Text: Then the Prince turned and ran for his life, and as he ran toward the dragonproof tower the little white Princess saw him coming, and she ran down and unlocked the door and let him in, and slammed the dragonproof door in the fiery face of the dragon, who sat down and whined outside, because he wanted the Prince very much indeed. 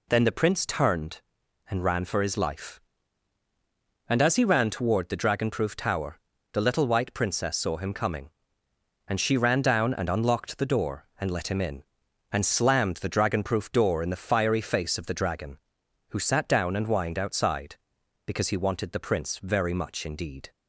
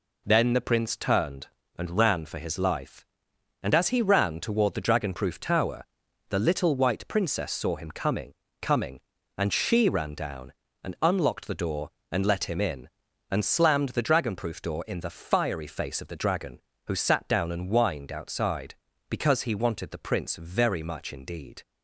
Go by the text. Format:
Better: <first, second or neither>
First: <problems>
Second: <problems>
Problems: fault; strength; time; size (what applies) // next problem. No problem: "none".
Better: first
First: pauses between "tower" and "the"; slight; at 6.1 s; 0.36 s long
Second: pauses between "tower" and "the"; noticeable; at 5.8 s; 0.46 s long // says "coming" twice; at 8.6 s